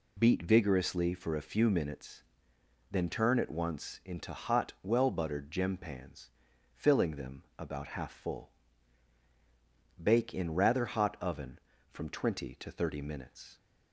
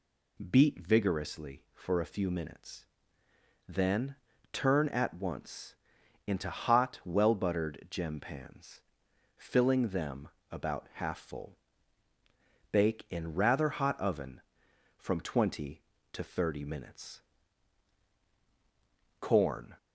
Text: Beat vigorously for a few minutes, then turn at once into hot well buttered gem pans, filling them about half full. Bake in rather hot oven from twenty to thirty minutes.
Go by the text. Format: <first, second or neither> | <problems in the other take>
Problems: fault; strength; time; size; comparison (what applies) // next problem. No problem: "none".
first | pauses between "then" and "turn"; at 4.1 s; 0.38 s long // pauses between "once" and "into"; noticeable; at 5.7 s; 0.54 s long // pauses between "them" and "about"; slight; at 10.2 s; 0.22 s long // goes on to say "CORN"; from 19.2 s on; 0.56 s long